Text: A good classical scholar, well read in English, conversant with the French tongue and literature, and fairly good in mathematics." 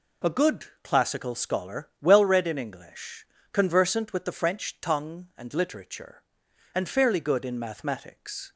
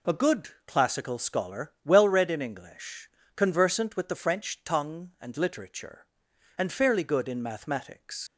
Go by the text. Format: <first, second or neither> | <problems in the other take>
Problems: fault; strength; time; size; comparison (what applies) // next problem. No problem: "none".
first | pauses between "good" and "classical"; slight; at 0.4 s; 0.18 s long; slight in the first // leaves "mathematics" unfinished; at 8.2 s; 90 ms